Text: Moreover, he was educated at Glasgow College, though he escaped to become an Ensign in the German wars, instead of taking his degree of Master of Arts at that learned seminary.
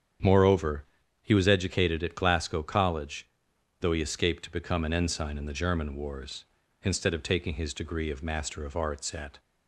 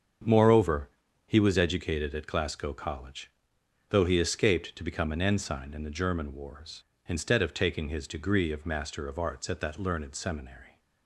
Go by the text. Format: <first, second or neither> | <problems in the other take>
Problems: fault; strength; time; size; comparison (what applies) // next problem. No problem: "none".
second | starts louder than the rest; strong; until 1.6 s; 8 dB; strong in the second // stops before "that learned seminary"; at 9.3 s